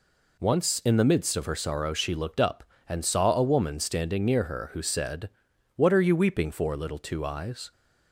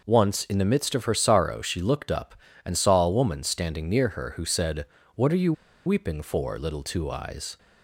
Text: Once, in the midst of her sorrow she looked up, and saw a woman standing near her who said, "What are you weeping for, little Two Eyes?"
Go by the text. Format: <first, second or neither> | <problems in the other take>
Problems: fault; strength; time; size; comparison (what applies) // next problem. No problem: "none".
first | pauses between "you" and "weeping"; slight; at 5.5 s; 0.33 s long